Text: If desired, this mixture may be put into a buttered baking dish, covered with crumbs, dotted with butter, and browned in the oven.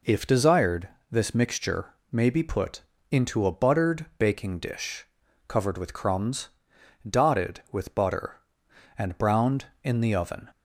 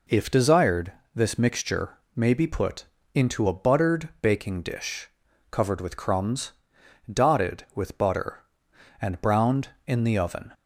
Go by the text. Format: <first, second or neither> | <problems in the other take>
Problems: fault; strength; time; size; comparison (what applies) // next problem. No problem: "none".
neither | pauses between "mixture" and "may"; slight; the same in both // pauses between "put" and "into"; slight; the same in both